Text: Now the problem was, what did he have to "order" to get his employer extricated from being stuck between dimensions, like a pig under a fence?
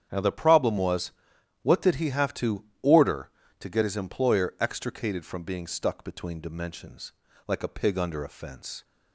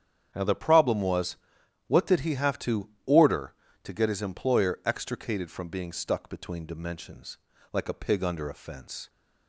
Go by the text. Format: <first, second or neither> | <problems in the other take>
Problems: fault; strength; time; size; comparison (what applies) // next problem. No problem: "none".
neither | starts louder than the rest; strong; the same in both // pauses between "to" and "order"; slight; the same in both